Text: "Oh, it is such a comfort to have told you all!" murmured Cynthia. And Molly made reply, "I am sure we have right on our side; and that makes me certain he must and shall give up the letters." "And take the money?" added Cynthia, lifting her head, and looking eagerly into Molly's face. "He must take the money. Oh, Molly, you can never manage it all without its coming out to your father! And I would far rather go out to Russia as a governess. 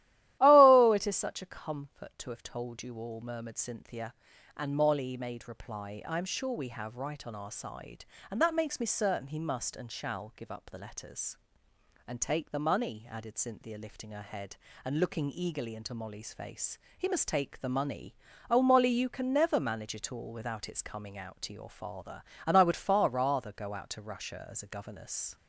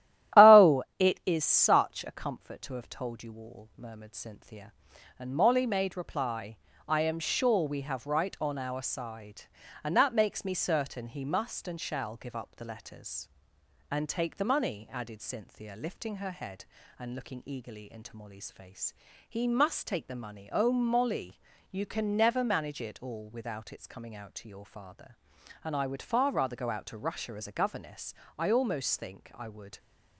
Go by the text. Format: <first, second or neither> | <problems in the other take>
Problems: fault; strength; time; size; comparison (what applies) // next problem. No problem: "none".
first | starts louder than the rest; strong; until 1.5 s; 13 dB; strong in the first // goes on to say "I almost think I would"; from 28.3 s on; 1.4 s long